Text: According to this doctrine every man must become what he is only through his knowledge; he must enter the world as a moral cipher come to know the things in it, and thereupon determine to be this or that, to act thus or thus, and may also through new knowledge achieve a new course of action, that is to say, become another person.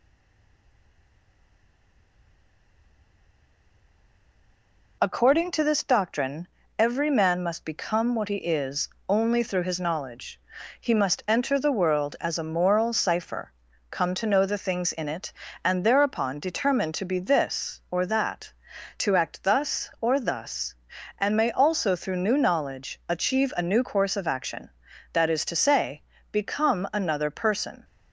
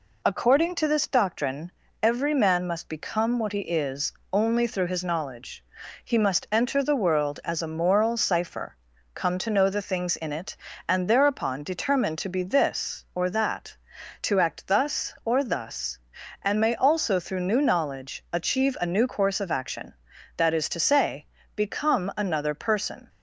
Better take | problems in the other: second | stays silent before the first word; strong; until 5.0 s; 5.0 s long // pauses between "doctrine" and "every"; slight; at 6.4 s; 0.28 s long; slight in the second // pauses between "is" and "only"; slight; at 8.8 s; 0.20 s long; slight in the second // pauses between "cipher" and "come"; at 13.5 s; 0.38 s long; also in the second

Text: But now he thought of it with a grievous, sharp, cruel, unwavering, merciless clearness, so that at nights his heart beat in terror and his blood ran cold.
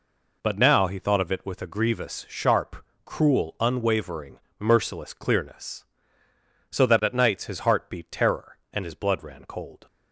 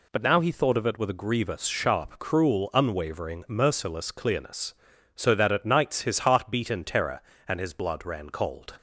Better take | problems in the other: second | skips "in"; at 8.0 s

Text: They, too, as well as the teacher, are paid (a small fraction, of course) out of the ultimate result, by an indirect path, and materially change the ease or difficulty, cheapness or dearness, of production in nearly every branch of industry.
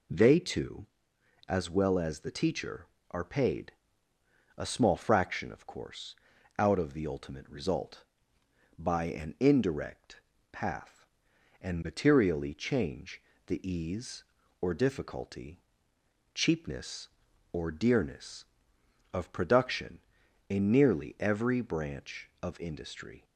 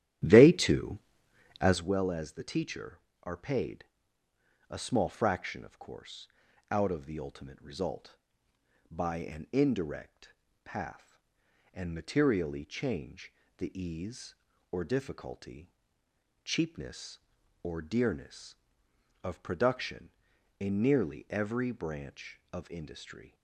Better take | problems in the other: first | starts louder than the rest; strong; until 1.9 s; 12 dB // pauses between "indirect" and "path"; slight; at 10.3 s; 0.32 s long; slight in the first // pauses between "change" and "the"; slight; at 13.3 s; 0.24 s long; slight in the first

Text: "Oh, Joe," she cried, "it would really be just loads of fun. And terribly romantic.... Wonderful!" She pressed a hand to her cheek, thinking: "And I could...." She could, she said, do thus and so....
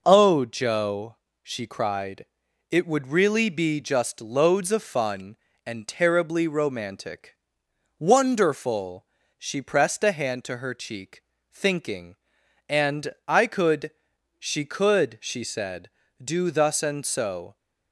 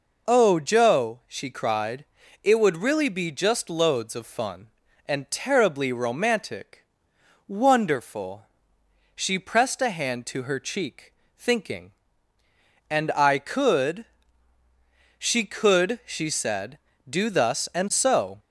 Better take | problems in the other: neither | none

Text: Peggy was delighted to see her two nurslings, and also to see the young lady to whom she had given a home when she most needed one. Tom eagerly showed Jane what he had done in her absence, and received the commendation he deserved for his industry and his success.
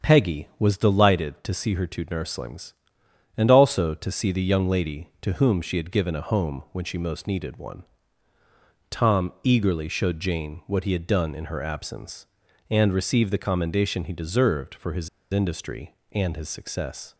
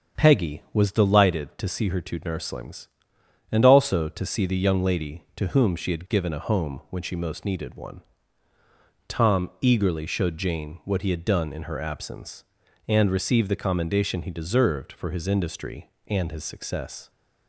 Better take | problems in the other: second | starts louder than the rest; strong; until 1.1 s; 7.5 dB; strong in the second // pauses between "his" and "industry"; slight; at 15.0 s; 0.23 s long

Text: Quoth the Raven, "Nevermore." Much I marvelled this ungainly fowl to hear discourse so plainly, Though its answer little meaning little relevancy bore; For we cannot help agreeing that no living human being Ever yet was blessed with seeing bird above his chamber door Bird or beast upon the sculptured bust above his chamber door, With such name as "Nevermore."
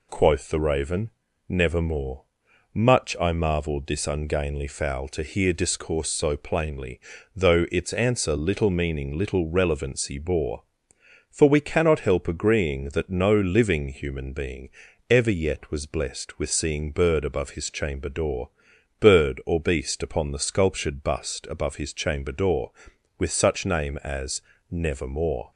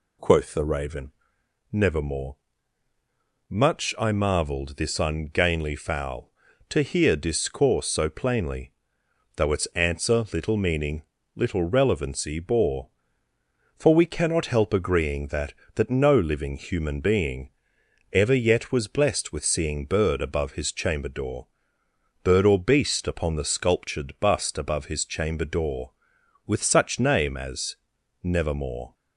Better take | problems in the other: first | pauses between "meaning" and "little"; slight; at 11.0 s; 0.32 s long // says "that" twice; at 15.7 s // pauses between "being" and "Ever"; noticeable; at 17.4 s; 0.62 s long; also in the first // pauses between "door" and "Bird"; noticeable; at 21.4 s; 0.76 s long; noticeable in the first // pauses between "as" and "Nevermore"; at 27.7 s; 0.44 s long; slight in the first

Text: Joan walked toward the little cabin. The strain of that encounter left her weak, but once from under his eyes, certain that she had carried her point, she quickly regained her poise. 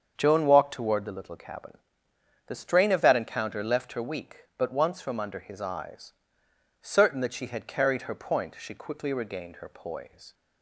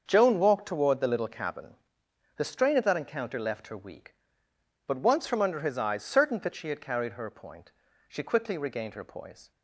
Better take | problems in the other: neither | starts louder than the rest; the same in both

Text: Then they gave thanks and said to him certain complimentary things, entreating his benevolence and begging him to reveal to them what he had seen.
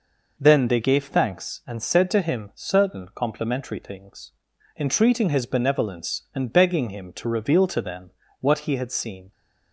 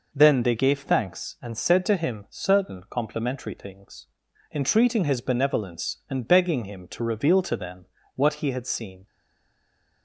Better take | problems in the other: first | pauses between "them" and "what"; slight; at 7.8 s; 0.30 s long; slight in the first // stays silent after the last word; from 9.0 s on; 1.0 s long

